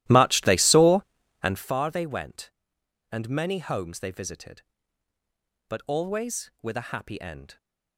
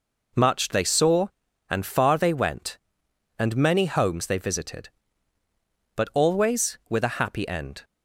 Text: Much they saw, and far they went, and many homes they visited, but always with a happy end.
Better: second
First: starts louder than the rest; strong; until 1.7 s; 15 dB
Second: none

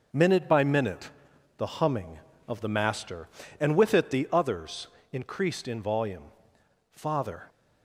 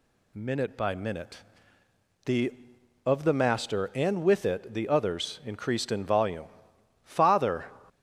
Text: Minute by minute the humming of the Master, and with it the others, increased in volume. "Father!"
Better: first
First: pauses between "minute" and "the"; noticeable; at 1.1 s; 0.48 s long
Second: pauses between "minute" and "the"; noticeable; at 1.3 s; 0.86 s long // skips "humming"; at 2.7 s

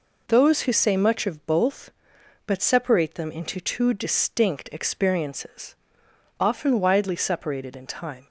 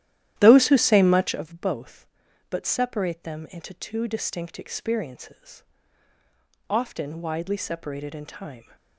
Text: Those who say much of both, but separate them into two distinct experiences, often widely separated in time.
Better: first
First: none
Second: starts louder than the rest; strong; until 1.4 s; 12.5 dB

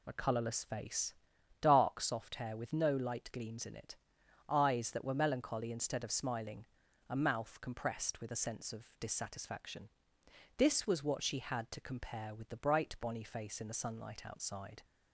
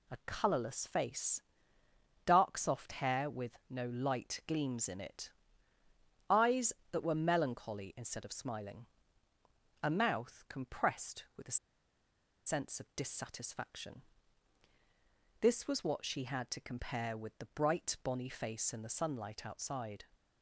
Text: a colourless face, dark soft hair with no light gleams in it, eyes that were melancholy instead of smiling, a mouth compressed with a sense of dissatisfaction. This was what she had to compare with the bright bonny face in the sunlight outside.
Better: first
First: none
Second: pauses between "a" and "sense"; noticeable; at 11.5 s; 0.88 s long

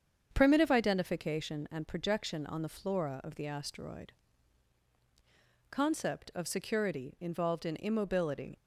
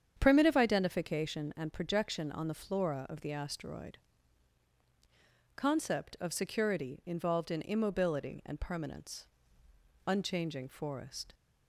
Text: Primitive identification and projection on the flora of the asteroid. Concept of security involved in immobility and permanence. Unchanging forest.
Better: second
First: starts louder than the rest; strong; until 1.3 s; 7.5 dB // stops before "and permanence Unchanging forest"; at 8.5 s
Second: starts louder than the rest; strong; until 1.2 s; 8 dB

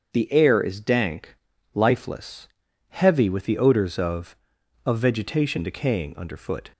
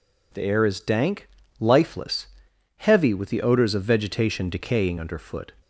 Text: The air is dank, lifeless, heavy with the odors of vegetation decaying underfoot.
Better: second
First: starts louder than the rest; until 1.1 s; 7 dB // says "of" twice; at 4.8 s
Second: none

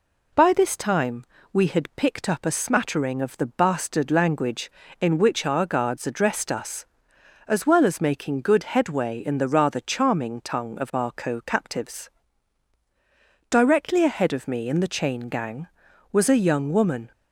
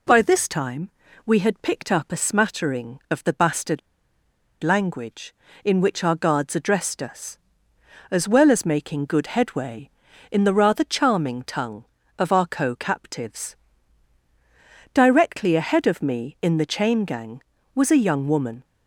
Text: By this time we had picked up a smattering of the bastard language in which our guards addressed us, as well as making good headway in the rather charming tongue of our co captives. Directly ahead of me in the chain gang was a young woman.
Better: first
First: pauses between "time" and "we"; slight; at 1.2 s; 0.28 s long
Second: pauses between "time" and "we"; slight; at 0.8 s; 0.36 s long // pauses between "bastard" and "language"; noticeable; at 3.7 s; 0.83 s long

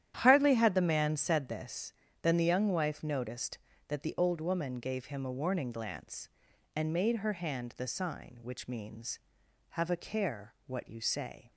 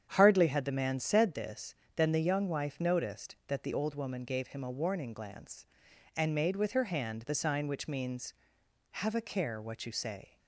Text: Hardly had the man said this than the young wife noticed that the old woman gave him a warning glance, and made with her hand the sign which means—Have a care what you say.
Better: second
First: starts louder than the rest; strong; until 1.2 s; 10.5 dB // skips "with"; at 7.1 s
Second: starts louder than the rest; strong; until 1.1 s; 8.5 dB

